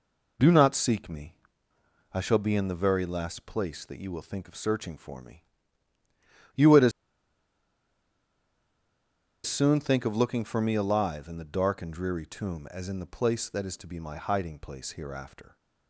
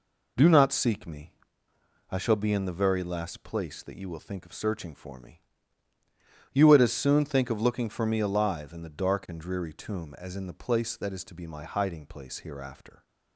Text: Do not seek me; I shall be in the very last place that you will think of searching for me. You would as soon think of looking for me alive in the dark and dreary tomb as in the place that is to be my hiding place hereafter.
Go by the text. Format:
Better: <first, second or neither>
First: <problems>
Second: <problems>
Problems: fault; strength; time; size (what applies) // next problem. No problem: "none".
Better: second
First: pauses between "as" and "soon"; strong; at 6.9 s; 2.5 s long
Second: none